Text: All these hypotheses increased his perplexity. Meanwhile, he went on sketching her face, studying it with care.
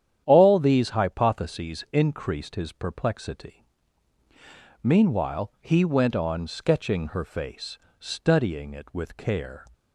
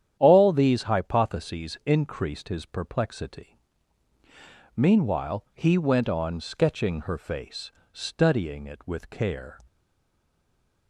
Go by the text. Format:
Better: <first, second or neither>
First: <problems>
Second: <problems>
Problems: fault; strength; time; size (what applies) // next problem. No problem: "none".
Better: first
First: starts louder than the rest; strong; until 1.2 s; 9.5 dB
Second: starts louder than the rest; strong; until 1.2 s; 9.5 dB // stays silent after the last word; noticeable; from 9.6 s on; 1.2 s long